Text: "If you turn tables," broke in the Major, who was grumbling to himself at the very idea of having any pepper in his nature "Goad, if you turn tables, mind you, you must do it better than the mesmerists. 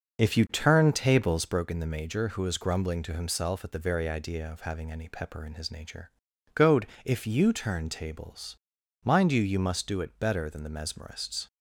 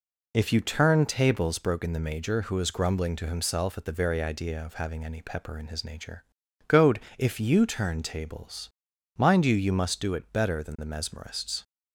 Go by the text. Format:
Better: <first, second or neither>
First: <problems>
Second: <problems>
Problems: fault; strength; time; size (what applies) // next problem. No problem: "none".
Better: second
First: starts louder than the rest; noticeable; until 1.7 s; 6 dB // pauses between "nature" and "Goad"; at 6.1 s; 0.44 s long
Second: pauses between "nature" and "Goad"; at 6.2 s; 0.44 s long